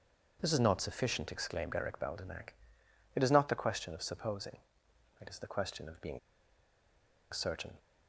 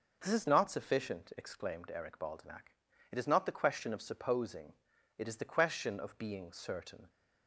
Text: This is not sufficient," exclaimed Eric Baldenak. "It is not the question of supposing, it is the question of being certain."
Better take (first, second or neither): second